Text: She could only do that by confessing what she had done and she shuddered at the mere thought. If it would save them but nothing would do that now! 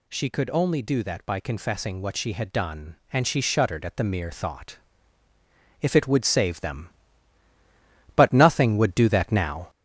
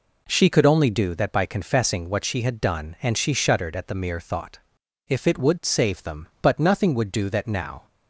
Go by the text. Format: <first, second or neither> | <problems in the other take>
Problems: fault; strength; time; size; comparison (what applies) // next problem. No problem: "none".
second | gets louder; noticeable; throughout; 4.5 dB